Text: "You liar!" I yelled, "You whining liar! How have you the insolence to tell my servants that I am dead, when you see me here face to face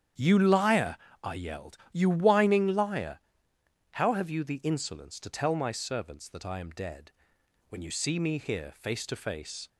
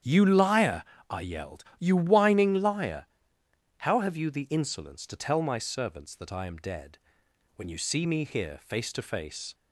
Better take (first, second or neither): neither